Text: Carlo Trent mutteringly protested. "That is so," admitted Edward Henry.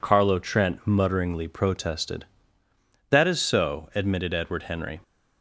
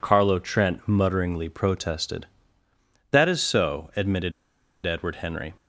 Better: first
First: none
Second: pauses between "admitted" and "Edward"; noticeable; at 4.3 s; 0.52 s long

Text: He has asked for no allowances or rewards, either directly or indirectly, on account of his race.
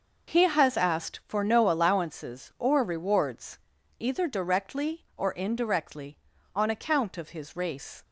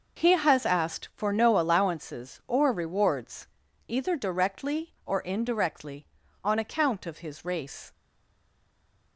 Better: first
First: none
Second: stays silent after the last word; noticeable; from 7.9 s on; 1.2 s long

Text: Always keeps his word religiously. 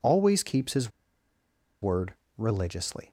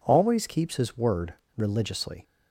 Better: second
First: pauses between "his" and "word"; noticeable; at 0.9 s; 0.91 s long // pauses between "word" and "religiously"; slight; at 2.1 s; 0.22 s long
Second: pauses between "word" and "religiously"; slight; at 1.3 s; 0.22 s long

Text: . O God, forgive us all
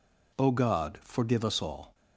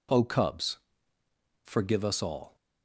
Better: first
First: none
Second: says "Cubs" for "God"; at 0.2 s

